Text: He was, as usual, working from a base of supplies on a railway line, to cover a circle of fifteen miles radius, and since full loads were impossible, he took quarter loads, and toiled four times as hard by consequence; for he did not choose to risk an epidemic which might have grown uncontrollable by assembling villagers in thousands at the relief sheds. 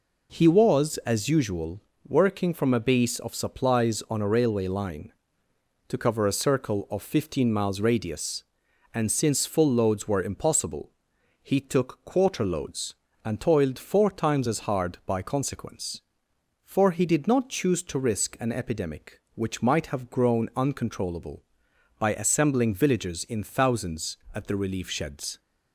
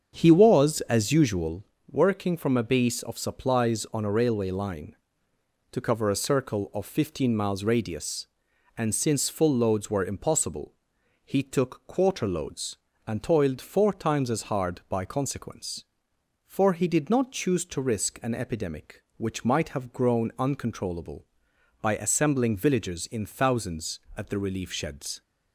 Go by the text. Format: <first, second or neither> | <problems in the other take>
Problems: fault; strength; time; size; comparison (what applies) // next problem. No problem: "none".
first | starts louder than the rest; until 1.6 s; 7 dB